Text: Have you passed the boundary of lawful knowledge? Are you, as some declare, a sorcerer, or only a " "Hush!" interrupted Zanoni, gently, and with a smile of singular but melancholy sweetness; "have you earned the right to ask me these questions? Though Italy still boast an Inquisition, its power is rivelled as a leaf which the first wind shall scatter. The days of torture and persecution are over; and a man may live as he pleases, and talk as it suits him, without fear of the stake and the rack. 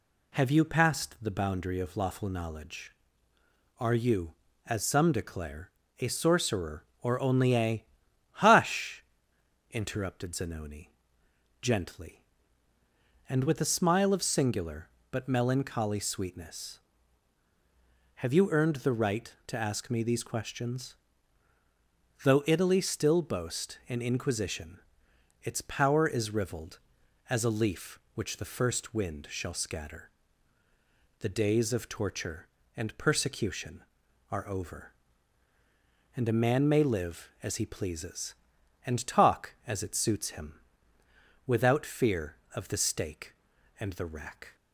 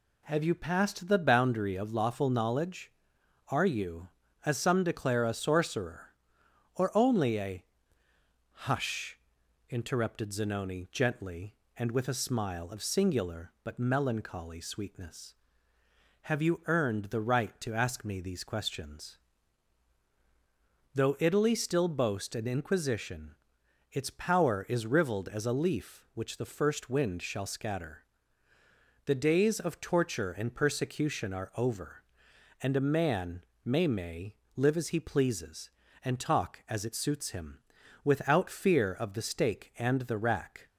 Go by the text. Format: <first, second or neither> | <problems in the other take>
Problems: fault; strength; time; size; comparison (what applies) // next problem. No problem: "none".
first | pauses between "man" and "may"; slight; at 33.4 s; 0.18 s long // says "may" twice; at 33.8 s